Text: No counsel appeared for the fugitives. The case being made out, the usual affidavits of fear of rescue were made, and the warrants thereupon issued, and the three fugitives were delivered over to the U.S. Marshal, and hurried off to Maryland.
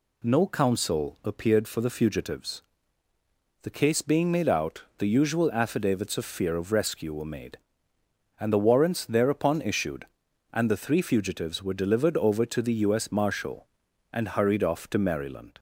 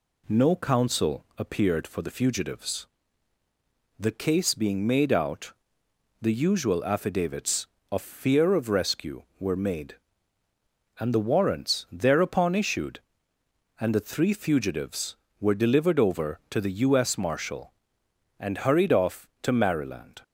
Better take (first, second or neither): neither